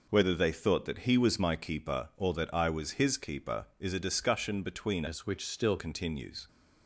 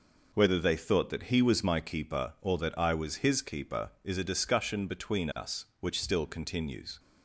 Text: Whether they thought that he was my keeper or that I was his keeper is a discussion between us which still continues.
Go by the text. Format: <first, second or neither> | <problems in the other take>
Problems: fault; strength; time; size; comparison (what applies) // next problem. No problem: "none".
second | changes voice from "us" to "still"; from 5.0 to 5.7 s; 0.7 s long